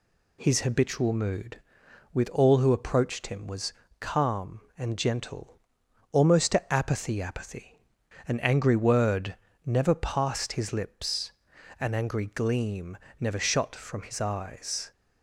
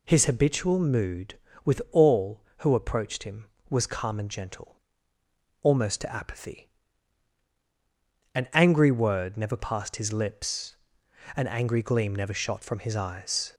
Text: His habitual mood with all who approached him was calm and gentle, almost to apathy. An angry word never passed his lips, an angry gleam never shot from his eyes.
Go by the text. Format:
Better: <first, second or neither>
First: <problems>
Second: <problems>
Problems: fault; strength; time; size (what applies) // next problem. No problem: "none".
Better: second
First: pauses between "was" and "calm"; slight; at 3.7 s; 0.26 s long // says "apathy" twice; at 7.2 s // pauses between "word" and "never"; slight; at 9.3 s; 0.30 s long // pauses between "gleam" and "never"; slight; at 12.9 s; 0.24 s long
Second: none